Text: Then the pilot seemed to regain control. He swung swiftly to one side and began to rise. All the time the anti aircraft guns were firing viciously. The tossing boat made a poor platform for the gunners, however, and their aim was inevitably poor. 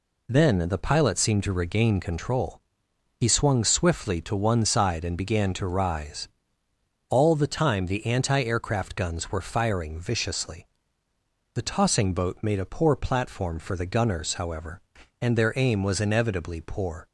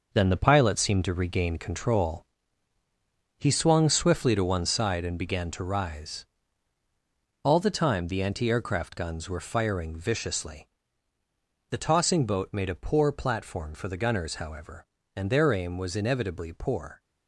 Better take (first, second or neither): first